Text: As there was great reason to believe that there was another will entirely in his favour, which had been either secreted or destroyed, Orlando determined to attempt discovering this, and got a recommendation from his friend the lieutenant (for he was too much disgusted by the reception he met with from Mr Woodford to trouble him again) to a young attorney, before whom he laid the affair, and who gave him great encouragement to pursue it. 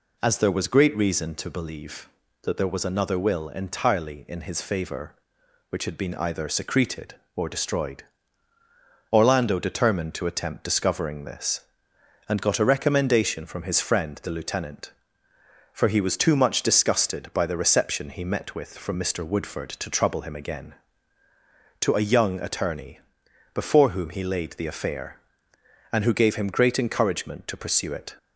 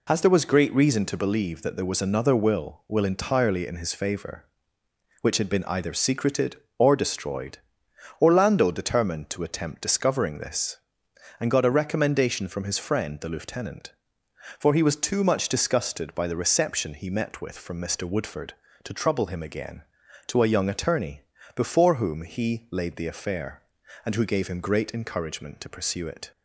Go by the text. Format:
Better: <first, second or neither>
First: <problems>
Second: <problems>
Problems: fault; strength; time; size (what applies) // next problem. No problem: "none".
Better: first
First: none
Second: says "will" twice; at 2.8 s